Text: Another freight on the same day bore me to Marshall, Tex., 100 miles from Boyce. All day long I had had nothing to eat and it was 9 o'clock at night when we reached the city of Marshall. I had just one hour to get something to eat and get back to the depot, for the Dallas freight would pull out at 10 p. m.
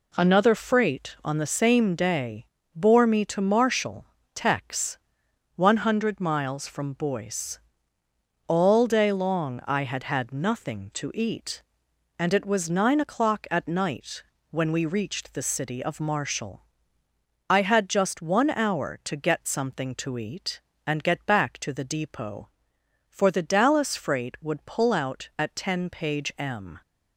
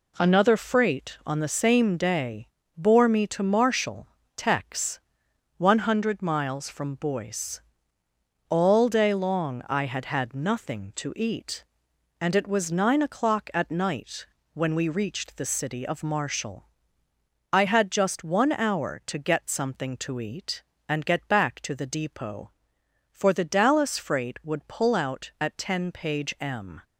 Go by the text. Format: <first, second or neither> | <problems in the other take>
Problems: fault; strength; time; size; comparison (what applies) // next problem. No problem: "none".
neither | pauses between "day" and "bore"; slight; the same in both // pauses between "night" and "when"; slight; the same in both